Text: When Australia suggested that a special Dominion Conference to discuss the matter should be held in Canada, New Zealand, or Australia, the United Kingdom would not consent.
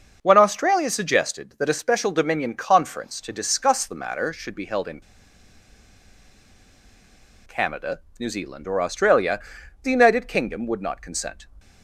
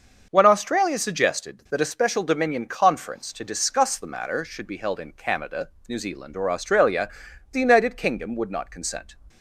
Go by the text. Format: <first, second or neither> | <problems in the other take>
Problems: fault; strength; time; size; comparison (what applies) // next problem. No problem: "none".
second | starts louder than the rest; until 1.2 s; 6.5 dB; also in the second // pauses between "in" and "Canada"; strong; at 4.9 s; 2.4 s long